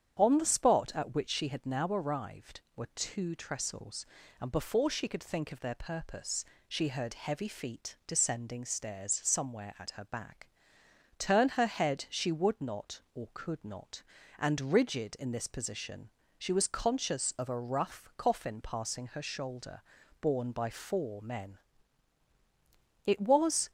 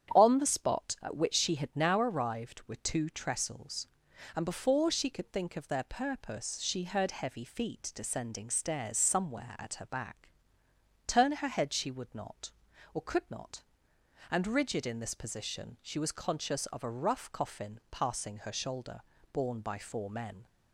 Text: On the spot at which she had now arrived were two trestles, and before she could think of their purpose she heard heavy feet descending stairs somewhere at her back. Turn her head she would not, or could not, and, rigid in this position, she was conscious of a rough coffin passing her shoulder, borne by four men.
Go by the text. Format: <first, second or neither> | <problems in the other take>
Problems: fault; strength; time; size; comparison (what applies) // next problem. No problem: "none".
second | starts louder than the rest; strong; until 1.1 s; 8.5 dB; strong in the second // pauses between "purpose" and "she"; slight; at 6.4 s; 0.24 s long // goes on to say "It was"; noticeable; from 23.0 s on; 0.64 s long